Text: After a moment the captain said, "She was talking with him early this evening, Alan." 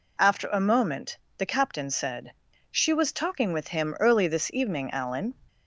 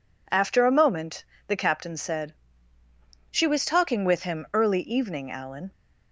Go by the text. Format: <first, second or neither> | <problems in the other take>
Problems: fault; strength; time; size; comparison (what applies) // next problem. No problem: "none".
first | pauses between "moment" and "the"; slight; at 1.2 s; 0.24 s long; slight in the first // skips "this"; at 4.8 s